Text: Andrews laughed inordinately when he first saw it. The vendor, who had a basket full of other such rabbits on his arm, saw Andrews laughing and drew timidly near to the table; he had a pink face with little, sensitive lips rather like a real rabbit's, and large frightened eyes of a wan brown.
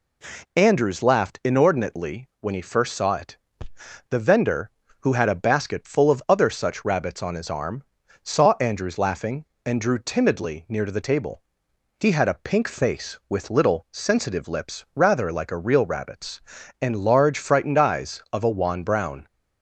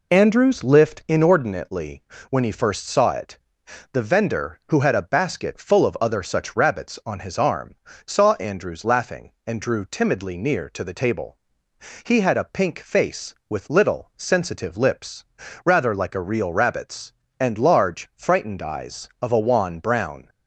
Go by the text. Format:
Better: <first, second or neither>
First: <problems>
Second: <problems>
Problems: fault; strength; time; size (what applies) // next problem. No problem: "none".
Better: first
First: none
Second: says "lift" for "laughed"; at 0.6 s // pauses between "inordinately" and "when"; slight; at 2.0 s; 0.30 s long // pauses between "lips" and "rather"; at 15.2 s; 0.40 s long